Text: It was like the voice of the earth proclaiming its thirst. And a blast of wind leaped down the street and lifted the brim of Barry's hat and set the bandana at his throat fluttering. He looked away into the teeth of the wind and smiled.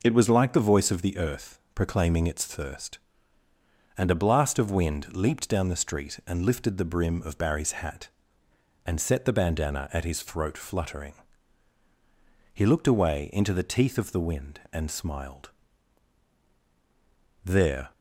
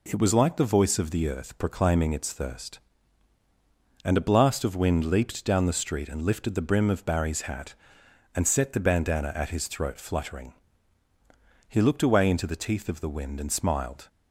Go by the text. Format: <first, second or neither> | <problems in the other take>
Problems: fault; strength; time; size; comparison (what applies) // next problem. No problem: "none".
second | pauses between "earth" and "proclaiming"; slight; at 1.5 s; 0.16 s long // goes on to say "There"; slight; from 17.4 s on; 0.48 s long